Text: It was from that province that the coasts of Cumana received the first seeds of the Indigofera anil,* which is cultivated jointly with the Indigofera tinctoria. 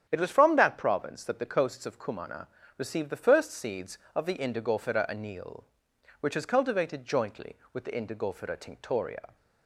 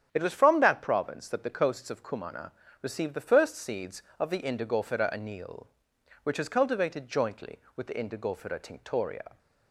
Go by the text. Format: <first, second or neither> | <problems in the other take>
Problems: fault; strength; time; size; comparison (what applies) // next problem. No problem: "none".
neither | starts louder than the rest; strong; the same in both // pauses between "Cumana" and "received"; slight; the same in both